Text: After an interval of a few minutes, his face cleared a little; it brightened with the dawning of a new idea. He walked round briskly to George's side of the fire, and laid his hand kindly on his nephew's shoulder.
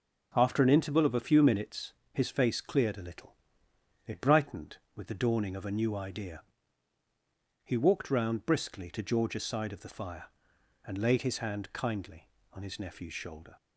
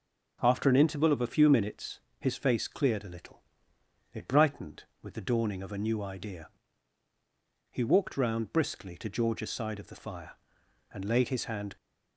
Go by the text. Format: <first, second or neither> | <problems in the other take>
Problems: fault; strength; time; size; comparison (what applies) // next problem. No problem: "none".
first | stops before "kindly on his nephew's shoulder"; at 11.7 s